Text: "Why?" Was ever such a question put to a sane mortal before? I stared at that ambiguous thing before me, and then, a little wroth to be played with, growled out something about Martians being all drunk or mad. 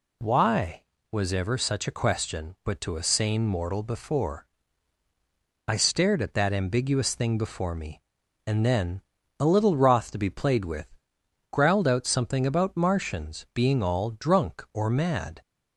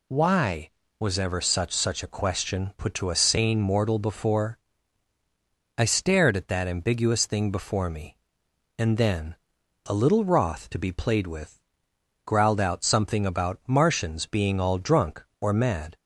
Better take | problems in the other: first | says "such" twice; at 1.7 s

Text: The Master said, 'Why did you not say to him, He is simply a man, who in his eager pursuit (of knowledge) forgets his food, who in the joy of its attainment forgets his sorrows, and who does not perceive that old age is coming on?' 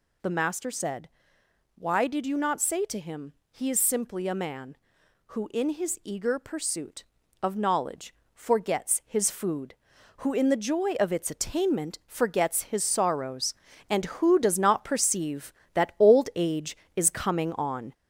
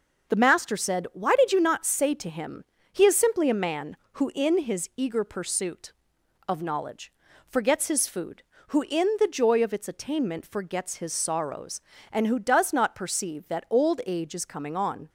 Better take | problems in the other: second | gets louder; noticeable; throughout; 5 dB

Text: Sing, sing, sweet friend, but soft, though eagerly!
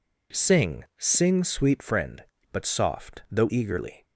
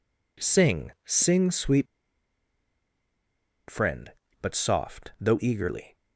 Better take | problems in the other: first | pauses between "sweet" and "friend"; strong; at 1.8 s; 1.8 s long

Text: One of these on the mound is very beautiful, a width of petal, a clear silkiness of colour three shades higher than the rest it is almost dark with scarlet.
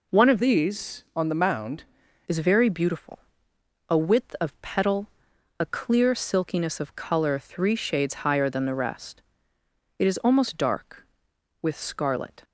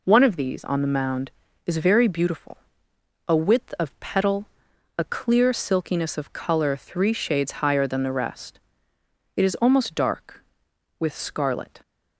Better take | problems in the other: second | changes voice from "these" to "mound"; from 0.4 to 1.8 s; 1.4 s long // pauses between "rest" and "it"; noticeable; at 9.2 s; 0.78 s long; noticeable in the second

